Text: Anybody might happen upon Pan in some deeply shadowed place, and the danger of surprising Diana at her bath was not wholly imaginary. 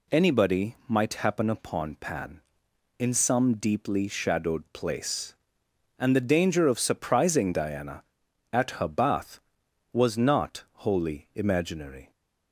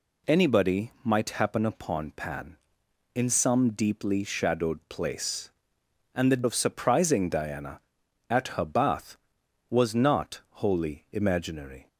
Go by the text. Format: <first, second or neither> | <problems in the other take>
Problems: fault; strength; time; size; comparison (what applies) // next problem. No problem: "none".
first | skips "danger"; at 6.4 s